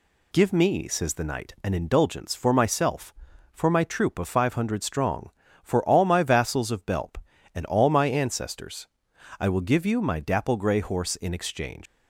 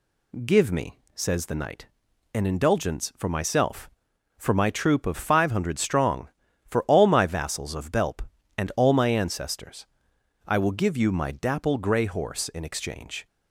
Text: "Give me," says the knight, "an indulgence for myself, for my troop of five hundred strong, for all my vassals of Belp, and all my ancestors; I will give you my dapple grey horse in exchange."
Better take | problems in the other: second | leaves "exchange" unfinished; at 11.8 s; 125 ms

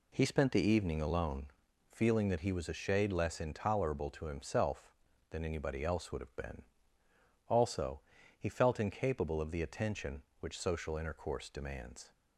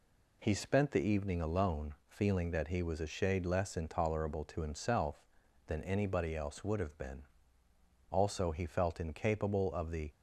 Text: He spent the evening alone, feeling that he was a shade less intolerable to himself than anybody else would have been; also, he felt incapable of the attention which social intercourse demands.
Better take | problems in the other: first | stops before "attention which social intercourse demands"; at 10.1 s

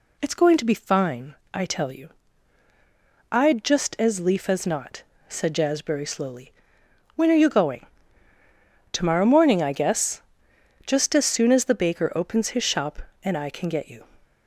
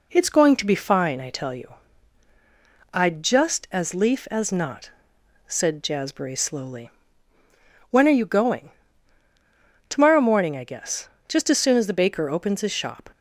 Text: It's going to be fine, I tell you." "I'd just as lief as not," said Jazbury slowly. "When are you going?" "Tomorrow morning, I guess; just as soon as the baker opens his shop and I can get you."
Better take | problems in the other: first | stops before "and I can get you"; at 13.1 s

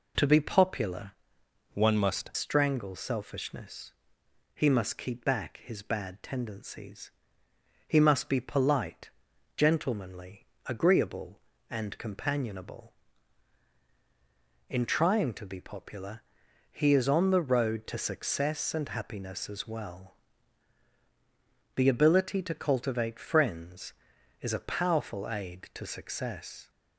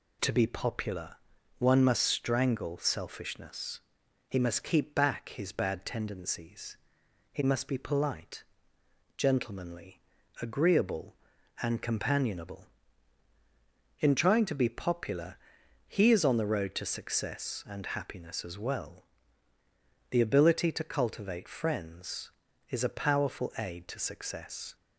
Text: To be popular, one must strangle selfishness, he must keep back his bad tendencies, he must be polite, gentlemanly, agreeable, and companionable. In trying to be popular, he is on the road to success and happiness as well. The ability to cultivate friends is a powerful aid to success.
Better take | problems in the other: second | changes voice from "one" to "must"; from 1.7 to 2.2 s; 0.5 s long

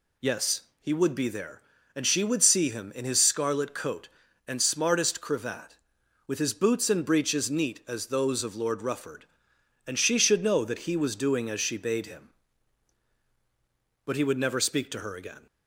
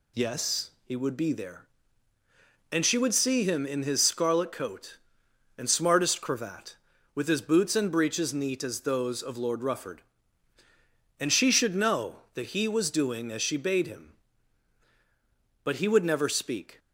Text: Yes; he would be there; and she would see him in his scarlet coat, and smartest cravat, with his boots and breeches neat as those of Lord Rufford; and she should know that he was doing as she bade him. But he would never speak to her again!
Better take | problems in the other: first | stops before "to her again"; at 16.7 s

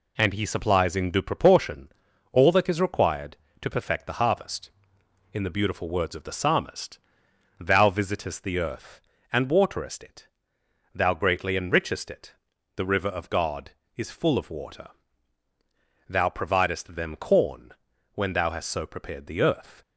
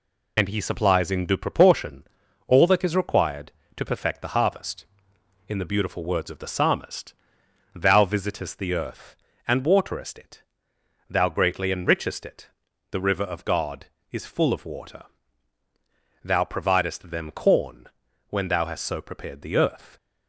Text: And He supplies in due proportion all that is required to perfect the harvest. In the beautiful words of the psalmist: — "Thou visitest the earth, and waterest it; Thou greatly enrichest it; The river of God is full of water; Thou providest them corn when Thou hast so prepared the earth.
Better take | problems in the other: first | loses the start of "And"; at 0.3 s; 50 ms // pauses between "proportion" and "all"; at 2.0 s; 0.44 s long; also in the first // pauses between "corn" and "when"; at 17.8 s; 0.42 s long; also in the first

